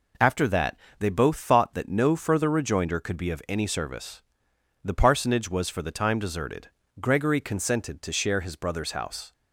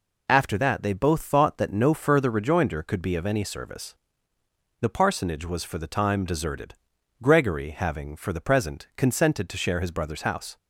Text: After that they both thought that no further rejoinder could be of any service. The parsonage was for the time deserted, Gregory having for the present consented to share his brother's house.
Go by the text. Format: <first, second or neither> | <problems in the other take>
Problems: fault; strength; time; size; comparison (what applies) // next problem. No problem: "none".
second | pauses between "that" and "they"; slight; at 0.7 s; 0.20 s long // skips "having for the present"; at 7.3 s